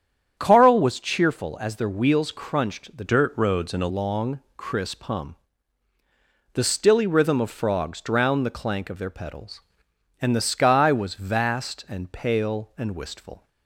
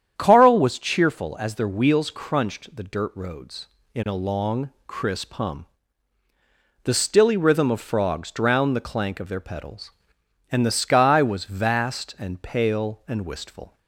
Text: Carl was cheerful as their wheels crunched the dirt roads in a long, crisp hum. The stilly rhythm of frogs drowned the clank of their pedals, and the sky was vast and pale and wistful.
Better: second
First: starts louder than the rest; strong; until 1.3 s; 8.5 dB // changes voice from "dirt" to "a"; from 3.0 to 3.8 s; 0.8 s long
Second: starts louder than the rest; strong; until 1.1 s; 9 dB

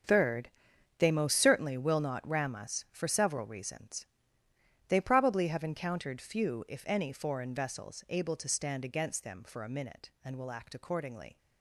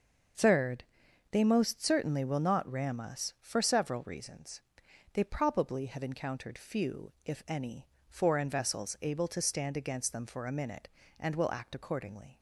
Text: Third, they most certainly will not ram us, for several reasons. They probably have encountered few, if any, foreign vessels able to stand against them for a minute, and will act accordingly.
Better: second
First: gets quieter; strong; throughout; 12 dB // starts louder than the rest; strong; until 1.5 s; 7 dB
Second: starts louder than the rest; until 1.8 s; 6 dB

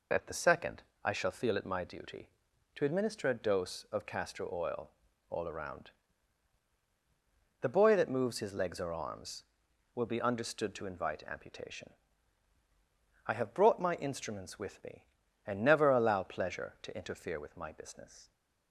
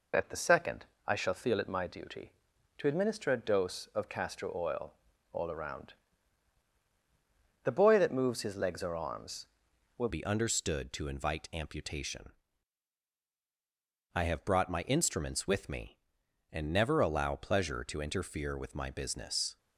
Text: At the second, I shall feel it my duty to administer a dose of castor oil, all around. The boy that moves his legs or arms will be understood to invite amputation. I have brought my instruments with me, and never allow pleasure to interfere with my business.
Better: first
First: none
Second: changes voice at "be"; from 10.0 s on; 9.5 s long

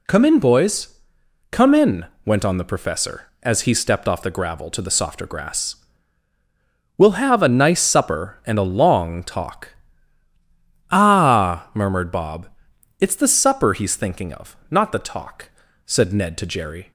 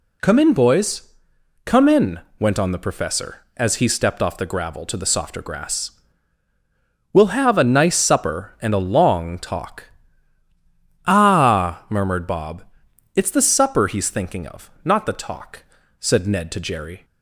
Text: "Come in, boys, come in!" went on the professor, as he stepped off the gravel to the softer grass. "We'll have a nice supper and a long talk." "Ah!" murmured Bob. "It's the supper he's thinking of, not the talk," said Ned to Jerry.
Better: neither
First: none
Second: none

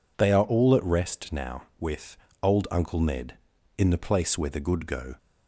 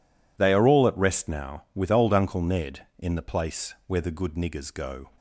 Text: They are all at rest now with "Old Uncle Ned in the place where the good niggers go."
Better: second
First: pauses between "with" and "Old"; slight; at 2.1 s; 0.24 s long // skips "niggers"; at 4.8 s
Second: none

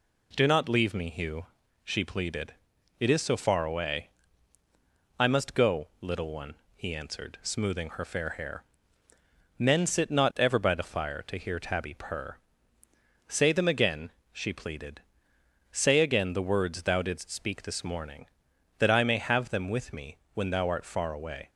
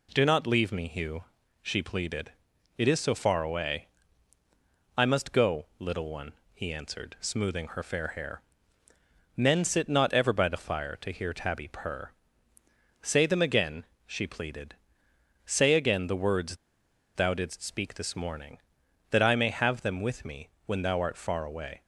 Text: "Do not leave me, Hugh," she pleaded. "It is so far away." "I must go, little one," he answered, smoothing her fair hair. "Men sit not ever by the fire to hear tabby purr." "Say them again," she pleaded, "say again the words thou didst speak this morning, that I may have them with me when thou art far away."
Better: first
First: pauses between "me" and "when"; slight; at 20.1 s; 0.16 s long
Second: pauses between "words" and "thou"; noticeable; at 16.5 s; 0.59 s long // pauses between "me" and "when"; slight; at 20.4 s; 0.16 s long

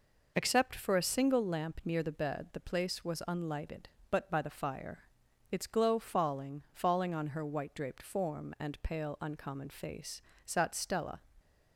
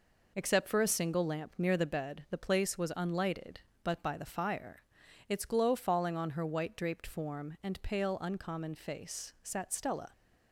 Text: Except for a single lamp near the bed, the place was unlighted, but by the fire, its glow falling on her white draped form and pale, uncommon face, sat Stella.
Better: second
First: says "falling" twice; at 6.7 s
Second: none

